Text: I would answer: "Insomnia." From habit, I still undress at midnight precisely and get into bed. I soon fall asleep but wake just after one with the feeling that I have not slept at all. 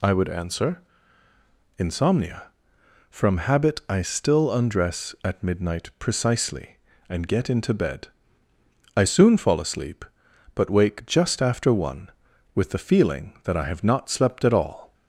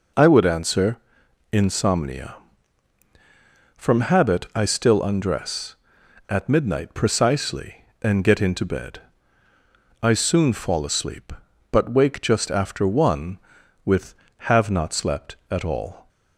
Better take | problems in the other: first | skips "the feeling that I"; at 14.3 s

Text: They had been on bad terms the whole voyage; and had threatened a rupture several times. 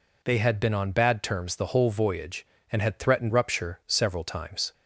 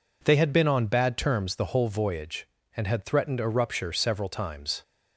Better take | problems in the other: second | skips "a"; at 3.3 s

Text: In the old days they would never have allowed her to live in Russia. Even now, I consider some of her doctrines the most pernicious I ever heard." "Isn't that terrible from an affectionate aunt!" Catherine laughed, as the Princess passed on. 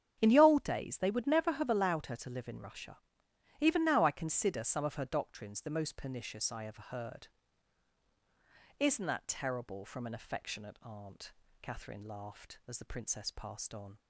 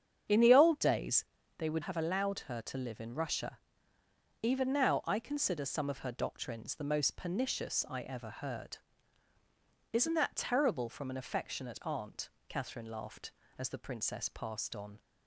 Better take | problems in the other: first | starts louder than the rest; strong; until 1.6 s; 8 dB; strong in the first // pauses between "days" and "they"; slight; at 1.2 s; 0.32 s long // skips "never"; at 1.8 s

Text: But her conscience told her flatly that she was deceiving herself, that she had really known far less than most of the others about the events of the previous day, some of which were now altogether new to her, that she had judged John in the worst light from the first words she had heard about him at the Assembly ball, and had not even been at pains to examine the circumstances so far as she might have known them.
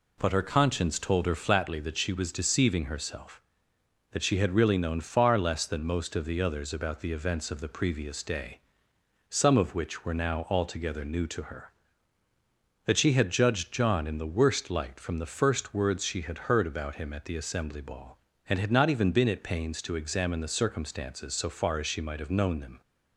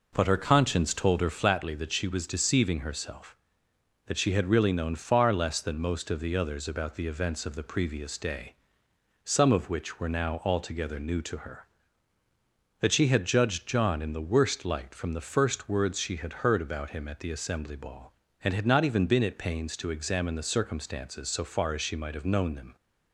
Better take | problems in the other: first | starts louder than the rest; noticeable; until 1.3 s; 4.5 dB

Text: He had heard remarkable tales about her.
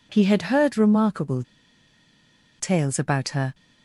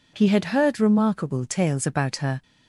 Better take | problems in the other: second | pauses between "remarkable" and "tales"; at 1.4 s; 1.1 s long

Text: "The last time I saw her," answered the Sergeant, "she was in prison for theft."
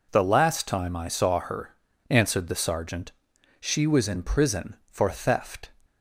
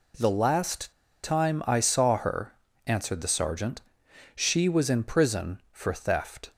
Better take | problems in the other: first | pauses between "last" and "time"; slight; at 0.9 s; 0.30 s long

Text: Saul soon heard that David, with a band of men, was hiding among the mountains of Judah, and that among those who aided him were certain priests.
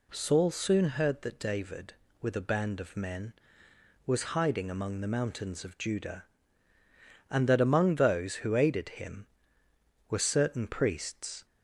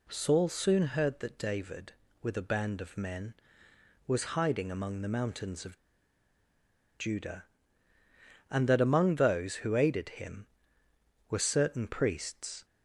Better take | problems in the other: first | pauses between "of" and "Judah"; at 5.7 s; 1.2 s long

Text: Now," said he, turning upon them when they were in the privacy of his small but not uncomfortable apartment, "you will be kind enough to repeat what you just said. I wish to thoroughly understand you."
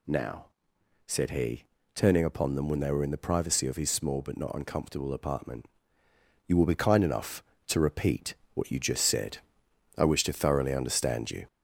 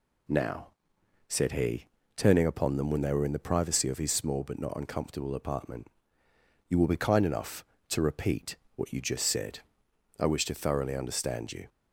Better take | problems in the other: second | gets louder; slight; throughout; 3 dB // pauses between "repeat" and "what"; slight; at 8.3 s; 0.18 s long; slight in the second

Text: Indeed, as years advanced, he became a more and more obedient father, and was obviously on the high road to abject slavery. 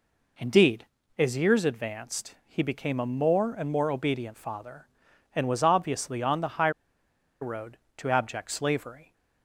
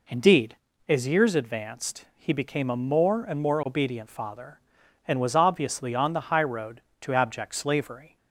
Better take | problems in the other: second | pauses between "high" and "road"; noticeable; at 6.7 s; 0.71 s long

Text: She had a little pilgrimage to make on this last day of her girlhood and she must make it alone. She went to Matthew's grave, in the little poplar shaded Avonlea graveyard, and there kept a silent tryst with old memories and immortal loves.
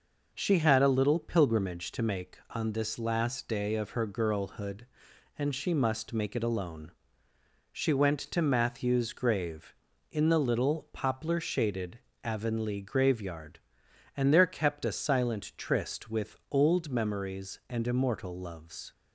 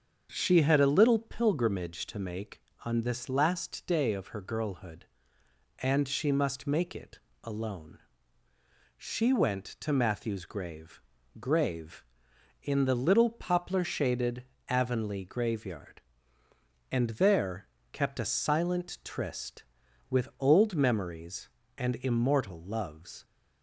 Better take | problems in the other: first | starts louder than the rest; until 1.3 s; 7 dB // pauses between "it" and "alone"; slight; at 7.1 s; 0.24 s long // says "grave" twice; at 11.4 s // pauses between "shaded" and "Avonlea"; slight; at 14.4 s; 0.24 s long; slight in the first // pauses between "there" and "kept"; slight; at 17.6 s; 0.24 s long

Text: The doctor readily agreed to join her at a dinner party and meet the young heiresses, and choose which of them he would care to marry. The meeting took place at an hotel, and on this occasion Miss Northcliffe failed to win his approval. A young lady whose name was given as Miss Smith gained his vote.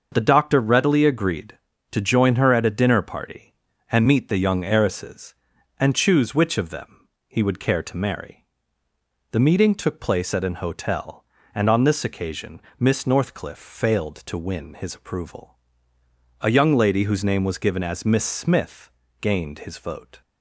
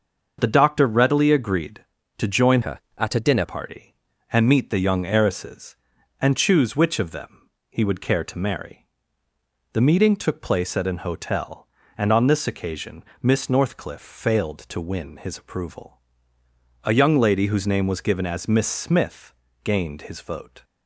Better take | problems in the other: first | starts louder than the rest; noticeable; until 1.4 s; 6 dB; also in the first // changes voice from "her" to "dinner"; from 2.6 to 3.4 s; 0.8 s long // pauses between "them" and "he"; slight; at 7.4 s; 0.20 s long; slight in the first // pauses between "occasion" and "Miss"; slight; at 13.0 s; 0.18 s long; slight in the first // pauses between "Smith" and "gained"; slight; at 19.3 s; 0.30 s long; slight in the first

